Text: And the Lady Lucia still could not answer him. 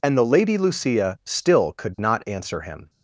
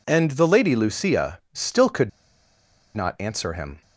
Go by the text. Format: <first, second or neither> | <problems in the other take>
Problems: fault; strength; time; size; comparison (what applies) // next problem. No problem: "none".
first | pauses between "could" and "not"; noticeable; at 2.0 s; 0.87 s long